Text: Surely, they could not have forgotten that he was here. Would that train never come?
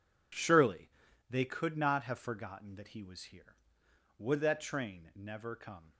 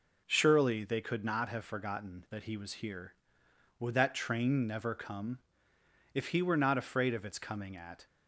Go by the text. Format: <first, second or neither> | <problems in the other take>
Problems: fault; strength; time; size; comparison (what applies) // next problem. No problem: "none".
first | goes on to say "If he were not afraid of its coming at"; strong; from 6.1 s on; 1.9 s long